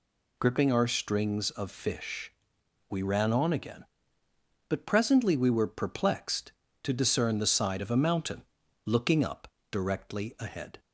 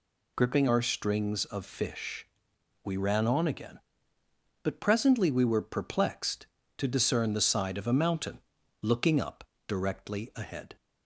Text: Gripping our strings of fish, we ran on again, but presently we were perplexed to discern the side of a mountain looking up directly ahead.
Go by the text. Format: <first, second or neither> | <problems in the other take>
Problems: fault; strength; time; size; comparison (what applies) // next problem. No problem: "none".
neither | pauses between "mountain" and "looking"; the same in both // pauses between "up" and "directly"; slight; the same in both